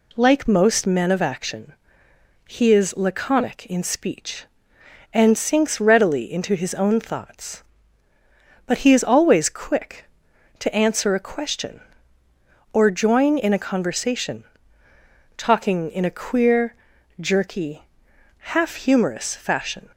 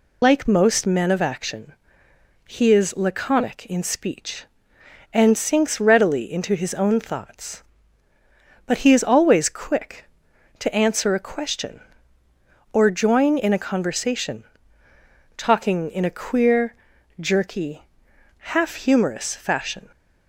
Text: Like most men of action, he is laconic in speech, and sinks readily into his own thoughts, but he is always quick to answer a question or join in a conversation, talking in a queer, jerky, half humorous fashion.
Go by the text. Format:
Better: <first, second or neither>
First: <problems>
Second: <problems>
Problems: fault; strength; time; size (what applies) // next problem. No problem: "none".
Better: first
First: none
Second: loses the start of "Like"; at 0.2 s; 115 ms